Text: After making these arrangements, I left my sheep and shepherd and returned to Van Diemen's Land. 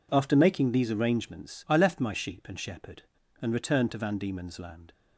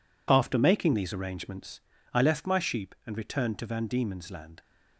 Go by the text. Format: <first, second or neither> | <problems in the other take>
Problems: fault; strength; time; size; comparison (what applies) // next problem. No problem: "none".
first | skips "and shepherd"; at 2.9 s